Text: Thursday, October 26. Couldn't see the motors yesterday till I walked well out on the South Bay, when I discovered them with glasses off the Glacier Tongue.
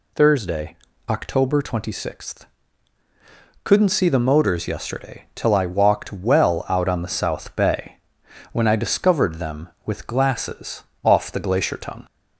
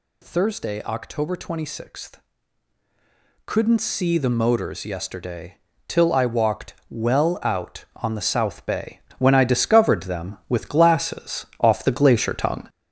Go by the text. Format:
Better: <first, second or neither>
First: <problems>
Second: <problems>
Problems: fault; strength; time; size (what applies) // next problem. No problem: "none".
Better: first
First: pauses between "glasses" and "off"; slight; at 10.8 s; 0.20 s long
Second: gets louder; noticeable; throughout; 6 dB // pauses between "yesterday" and "till"; slight; at 5.5 s; 0.30 s long // pauses between "glasses" and "off"; slight; at 11.4 s; 0.16 s long